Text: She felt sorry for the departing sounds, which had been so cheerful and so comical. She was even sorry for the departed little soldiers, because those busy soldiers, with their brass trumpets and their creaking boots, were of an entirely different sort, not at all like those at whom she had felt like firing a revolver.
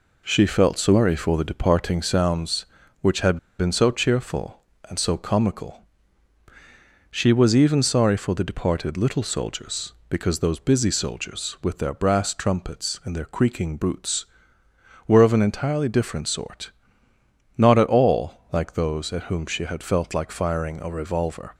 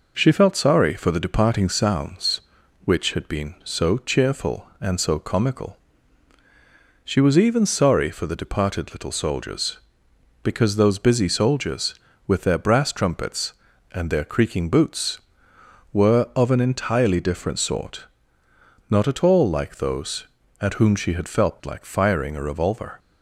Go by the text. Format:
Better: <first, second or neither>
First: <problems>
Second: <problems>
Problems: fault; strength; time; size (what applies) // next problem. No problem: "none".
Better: second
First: pauses between "had" and "been"; slight; at 3.3 s; 0.22 s long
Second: none